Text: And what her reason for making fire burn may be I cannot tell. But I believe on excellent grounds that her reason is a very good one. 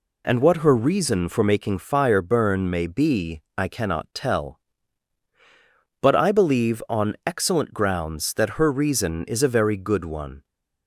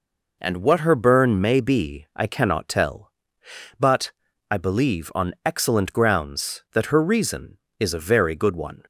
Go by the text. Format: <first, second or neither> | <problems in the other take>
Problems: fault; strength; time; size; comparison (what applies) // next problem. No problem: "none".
first | skips "reason for making fire"; at 0.9 s // pauses between "But" and "I"; at 4.1 s; 0.38 s long